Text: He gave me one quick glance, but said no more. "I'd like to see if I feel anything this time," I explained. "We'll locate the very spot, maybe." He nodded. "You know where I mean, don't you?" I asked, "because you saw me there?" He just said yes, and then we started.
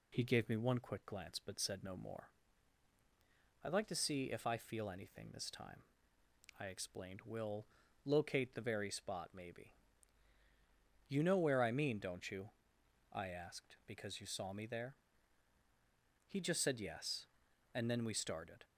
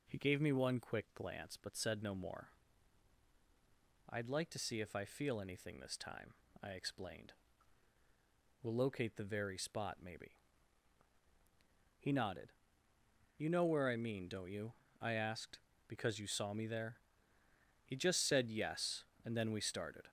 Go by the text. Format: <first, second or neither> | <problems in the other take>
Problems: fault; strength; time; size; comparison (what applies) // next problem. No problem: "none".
second | pauses between "We'll" and "locate"; at 7.6 s; 0.40 s long // skips "He nodded"; at 10.3 s